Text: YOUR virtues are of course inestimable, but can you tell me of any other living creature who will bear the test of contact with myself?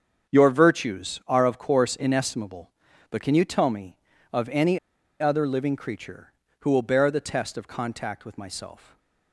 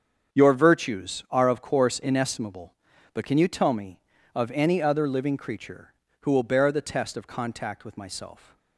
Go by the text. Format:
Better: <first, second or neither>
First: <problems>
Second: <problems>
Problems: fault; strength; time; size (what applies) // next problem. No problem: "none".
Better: second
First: starts louder than the rest; until 1.3 s; 7 dB // pauses between "any" and "other"; at 4.7 s; 0.42 s long // stays silent after the last word; slight; from 8.7 s on; 0.6 s long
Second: starts louder than the rest; until 1.3 s; 7 dB